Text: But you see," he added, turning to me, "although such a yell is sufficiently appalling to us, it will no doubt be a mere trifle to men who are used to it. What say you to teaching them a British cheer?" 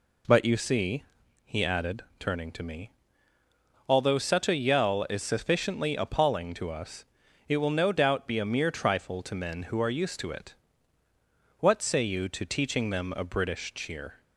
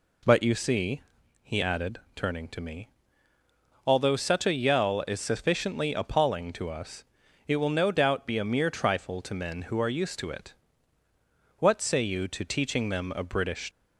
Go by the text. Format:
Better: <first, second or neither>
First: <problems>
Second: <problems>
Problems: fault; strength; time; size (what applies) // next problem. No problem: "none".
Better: first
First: none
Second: stops before "cheer"; at 13.7 s